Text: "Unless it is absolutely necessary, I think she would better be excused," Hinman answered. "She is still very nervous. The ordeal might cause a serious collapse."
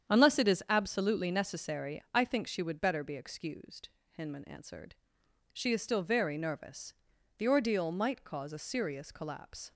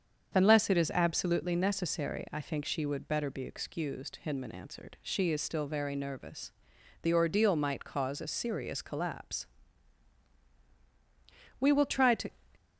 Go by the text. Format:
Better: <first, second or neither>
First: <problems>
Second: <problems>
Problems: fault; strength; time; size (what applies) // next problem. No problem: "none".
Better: first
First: starts louder than the rest; strong; until 1.1 s; 8.5 dB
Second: starts louder than the rest; strong; until 1.3 s; 7 dB // goes on to say "We will try to"; noticeable; from 11.6 s on; 0.70 s long